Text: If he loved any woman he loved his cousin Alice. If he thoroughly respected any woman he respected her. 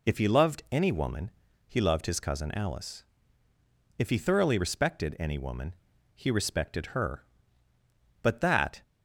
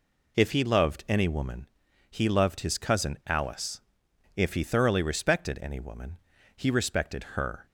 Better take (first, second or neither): second